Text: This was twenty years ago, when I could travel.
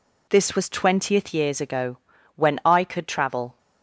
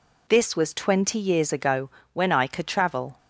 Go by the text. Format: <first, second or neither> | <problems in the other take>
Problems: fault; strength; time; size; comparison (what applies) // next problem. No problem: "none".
second | says "twentieth" for "twenty"; at 0.6 s